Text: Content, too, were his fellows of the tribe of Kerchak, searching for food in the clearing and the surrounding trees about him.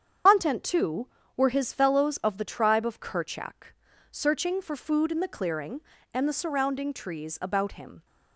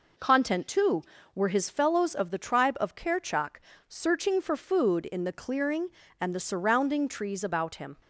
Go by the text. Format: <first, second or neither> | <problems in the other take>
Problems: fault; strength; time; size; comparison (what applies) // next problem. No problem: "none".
second | loses the start of "Content"; at 0.2 s; 85 ms // starts louder than the rest; strong; until 1.5 s; 8 dB